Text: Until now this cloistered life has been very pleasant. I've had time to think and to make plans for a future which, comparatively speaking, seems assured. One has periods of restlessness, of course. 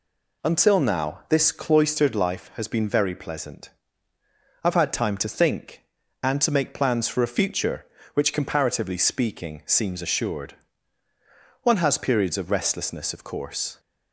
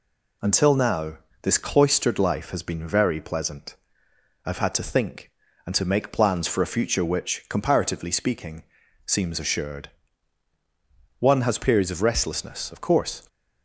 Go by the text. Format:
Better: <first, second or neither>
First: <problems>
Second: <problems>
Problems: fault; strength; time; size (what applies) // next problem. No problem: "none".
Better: first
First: none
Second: pauses between "now" and "this"; slight; at 1.1 s; 0.26 s long // skips "time"; at 4.7 s